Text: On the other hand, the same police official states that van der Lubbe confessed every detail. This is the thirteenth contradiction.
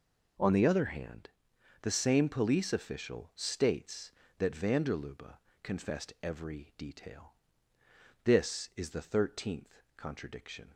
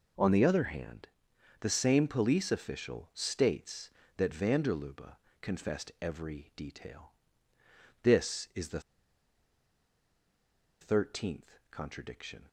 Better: first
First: pauses between "Lubbe" and "confessed"; slight; at 5.3 s; 0.26 s long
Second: pauses between "Lubbe" and "confessed"; slight; at 5.1 s; 0.26 s long // pauses between "the" and "thirteenth"; strong; at 8.7 s; 2.0 s long

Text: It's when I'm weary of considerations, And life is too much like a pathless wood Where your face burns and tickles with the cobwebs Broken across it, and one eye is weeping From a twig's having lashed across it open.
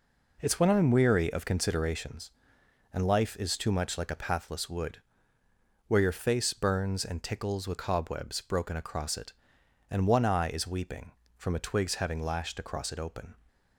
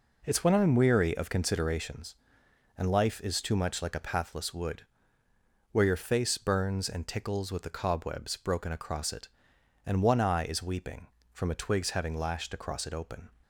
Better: second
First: pauses between "wood" and "Where"; noticeable; at 5.0 s; 0.88 s long // skips "the"; at 7.7 s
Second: pauses between "wood" and "Where"; noticeable; at 4.8 s; 0.88 s long

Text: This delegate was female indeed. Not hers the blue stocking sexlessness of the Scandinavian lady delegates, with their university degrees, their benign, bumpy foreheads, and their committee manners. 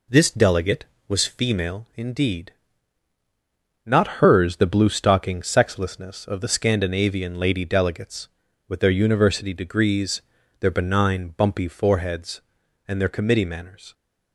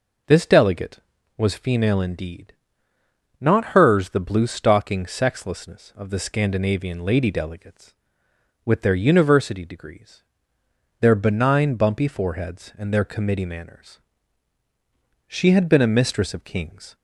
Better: first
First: none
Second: goes on to say "She had been a mistress of kings"; strong; from 15.2 s on; 1.6 s long

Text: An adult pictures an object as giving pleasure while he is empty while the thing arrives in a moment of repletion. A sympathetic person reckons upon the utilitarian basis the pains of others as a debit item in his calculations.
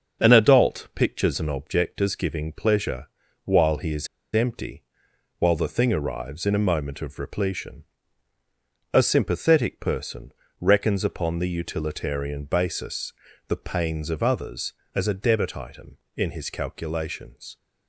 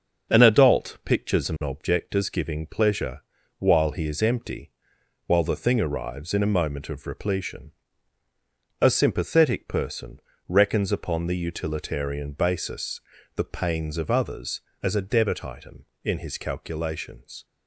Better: second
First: starts louder than the rest; until 1.2 s; 6.5 dB // pauses between "pleasure" and "while"; slight; at 3.0 s; 0.34 s long // pauses between "is" and "empty"; slight; at 4.0 s; 0.26 s long // pauses between "empty" and "while"; noticeable; at 4.8 s; 0.56 s long // pauses between "person" and "reckons"; slight; at 10.3 s; 0.28 s long // pauses between "basis" and "the"; slight; at 13.1 s; 0.36 s long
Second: starts louder than the rest; until 1.3 s; 6.5 dB // pauses between "pleasure" and "while"; slight; at 3.2 s; 0.34 s long // pauses between "empty" and "while"; noticeable; at 4.6 s; 0.56 s long // pauses between "person" and "reckons"; slight; at 10.1 s; 0.28 s long // pauses between "basis" and "the"; slight; at 13.0 s; 0.36 s long

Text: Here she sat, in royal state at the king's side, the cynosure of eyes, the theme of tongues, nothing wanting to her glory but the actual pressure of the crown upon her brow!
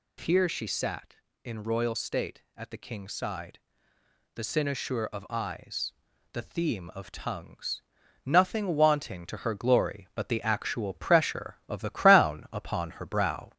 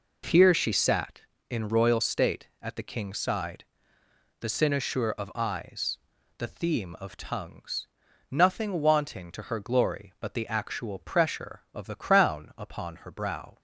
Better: second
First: gets louder; slight; throughout; 2 dB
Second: none

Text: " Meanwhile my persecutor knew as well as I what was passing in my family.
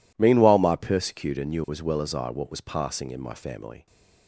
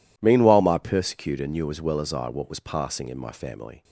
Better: neither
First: none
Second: none

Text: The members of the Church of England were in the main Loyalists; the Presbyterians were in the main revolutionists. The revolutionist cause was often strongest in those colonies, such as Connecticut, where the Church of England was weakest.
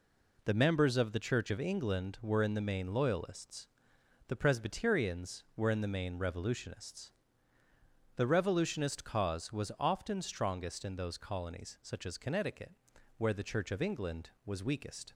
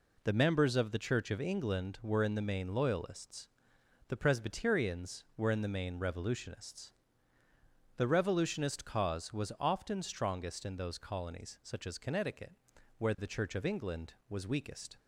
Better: neither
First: none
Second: none

